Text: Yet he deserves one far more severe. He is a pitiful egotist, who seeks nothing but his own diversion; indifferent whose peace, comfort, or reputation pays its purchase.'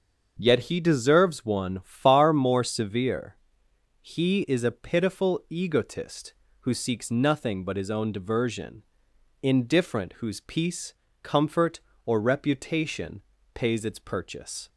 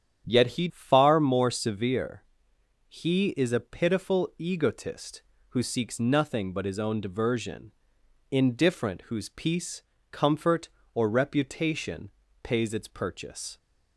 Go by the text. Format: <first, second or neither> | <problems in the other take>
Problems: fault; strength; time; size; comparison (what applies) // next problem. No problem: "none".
first | starts louder than the rest; strong; until 1.2 s; 9.5 dB; also in the first // skips "deserves one"; at 0.6 s // pauses between "reputation" and "pays"; slight; at 12.1 s; 0.32 s long; slight in the first